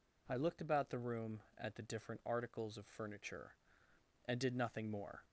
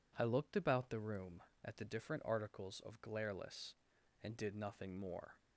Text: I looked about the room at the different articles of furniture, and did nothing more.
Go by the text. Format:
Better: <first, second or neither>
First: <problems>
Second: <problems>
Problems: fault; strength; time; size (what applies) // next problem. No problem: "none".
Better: first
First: none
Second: says "glareless" for "furniture"; at 3.0 s